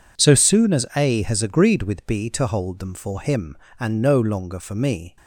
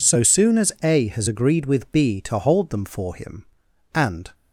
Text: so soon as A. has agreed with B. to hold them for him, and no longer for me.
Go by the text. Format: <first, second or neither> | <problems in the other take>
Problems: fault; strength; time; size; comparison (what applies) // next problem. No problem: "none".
first | stops before "no longer for me"; at 4.3 s